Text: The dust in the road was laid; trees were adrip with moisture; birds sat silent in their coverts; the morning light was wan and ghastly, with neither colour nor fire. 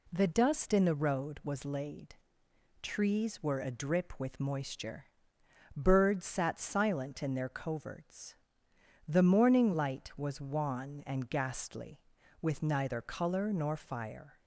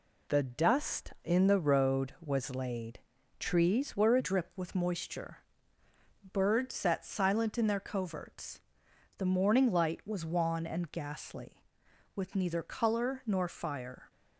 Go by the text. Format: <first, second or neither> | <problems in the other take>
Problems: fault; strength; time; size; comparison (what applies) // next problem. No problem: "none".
first | changes voice at "adrip"; from 4.1 s on; 9.9 s long